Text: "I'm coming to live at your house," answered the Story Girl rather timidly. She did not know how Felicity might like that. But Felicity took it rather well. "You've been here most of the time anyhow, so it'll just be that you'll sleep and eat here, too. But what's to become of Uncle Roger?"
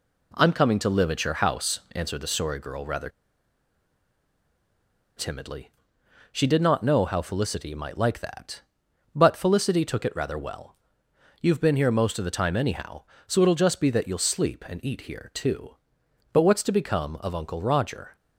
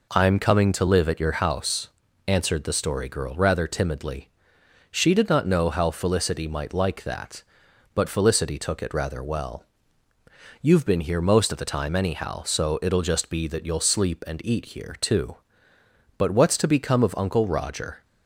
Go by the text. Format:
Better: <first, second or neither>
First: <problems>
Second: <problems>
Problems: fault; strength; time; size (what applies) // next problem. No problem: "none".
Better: second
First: pauses between "rather" and "timidly"; strong; at 3.0 s; 2.0 s long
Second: none